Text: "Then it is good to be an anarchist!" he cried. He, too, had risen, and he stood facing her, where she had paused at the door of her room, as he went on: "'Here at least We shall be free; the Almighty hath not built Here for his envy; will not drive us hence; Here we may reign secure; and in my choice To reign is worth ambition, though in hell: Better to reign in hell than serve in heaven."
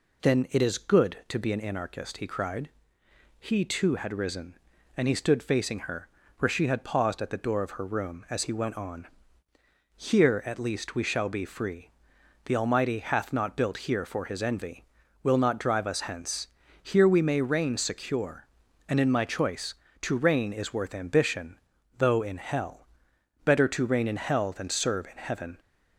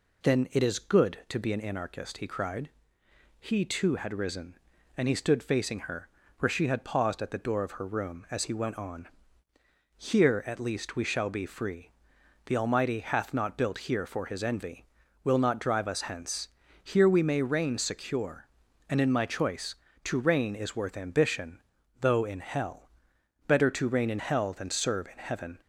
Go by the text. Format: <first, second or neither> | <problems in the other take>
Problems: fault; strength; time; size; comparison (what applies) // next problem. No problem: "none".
neither | none